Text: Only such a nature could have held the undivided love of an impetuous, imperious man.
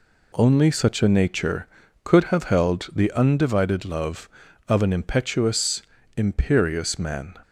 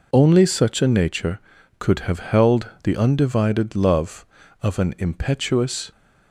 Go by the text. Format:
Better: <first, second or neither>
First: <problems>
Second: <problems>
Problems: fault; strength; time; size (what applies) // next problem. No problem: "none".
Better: first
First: none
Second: pauses between "held" and "the"; slight; at 2.6 s; 0.16 s long // stops before "imperious man"; at 5.9 s